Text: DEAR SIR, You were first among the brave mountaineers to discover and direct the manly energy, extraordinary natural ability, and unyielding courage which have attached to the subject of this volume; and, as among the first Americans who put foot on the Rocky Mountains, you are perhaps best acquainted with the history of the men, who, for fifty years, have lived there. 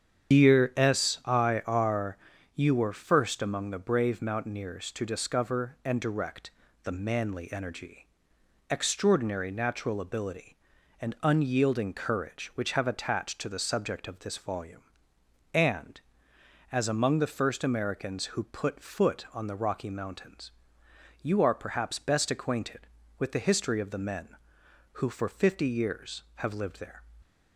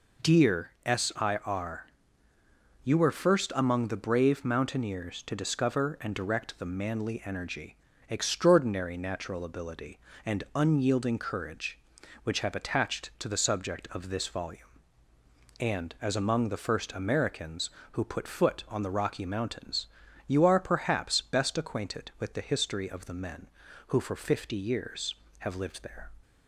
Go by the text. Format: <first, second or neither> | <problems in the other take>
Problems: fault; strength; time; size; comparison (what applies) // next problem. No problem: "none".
second | loses the start of "DEAR"; at 0.3 s; 145 ms // starts louder than the rest; strong; until 1.4 s; 8.5 dB // pauses between "direct" and "the"; slight; at 6.5 s; 0.32 s long